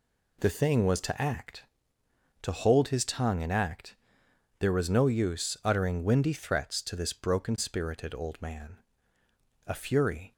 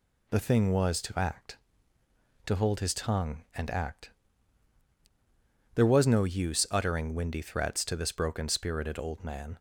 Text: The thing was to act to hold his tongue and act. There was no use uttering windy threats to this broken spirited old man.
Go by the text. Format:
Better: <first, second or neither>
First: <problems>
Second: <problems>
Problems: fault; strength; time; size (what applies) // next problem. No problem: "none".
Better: second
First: goes on to say "A fury"; noticeable; from 9.6 s on; 0.66 s long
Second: none